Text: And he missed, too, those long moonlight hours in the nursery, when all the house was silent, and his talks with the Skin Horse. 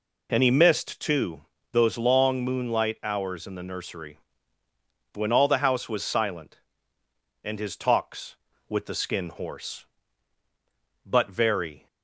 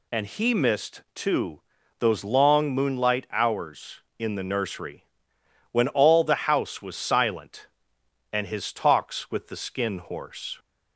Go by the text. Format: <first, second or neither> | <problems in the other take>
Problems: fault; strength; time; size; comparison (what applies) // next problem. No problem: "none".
second | goes on to say "But very"; noticeable; from 11.0 s on; 0.82 s long